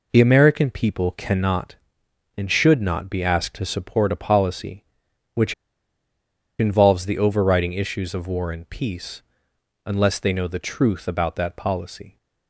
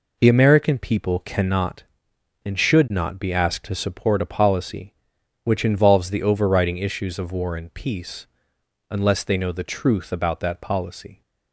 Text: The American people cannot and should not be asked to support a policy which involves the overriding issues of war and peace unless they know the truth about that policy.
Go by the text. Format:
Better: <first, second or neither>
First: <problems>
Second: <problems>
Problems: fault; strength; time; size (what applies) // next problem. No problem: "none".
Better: second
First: pauses between "which" and "involves"; at 5.5 s; 1.0 s long // pauses between "peace" and "unless"; noticeable; at 9.2 s; 0.62 s long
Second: pauses between "peace" and "unless"; noticeable; at 8.2 s; 0.62 s long